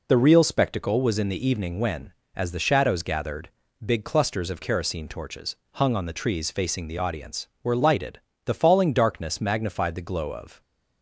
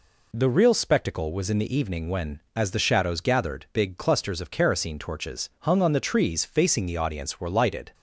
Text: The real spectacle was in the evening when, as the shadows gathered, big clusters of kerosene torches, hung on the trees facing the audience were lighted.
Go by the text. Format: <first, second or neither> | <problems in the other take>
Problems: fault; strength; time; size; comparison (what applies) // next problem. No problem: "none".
second | goes on to say "The falling darkness magnified the glow of"; strong; from 8.4 s on; 2.1 s long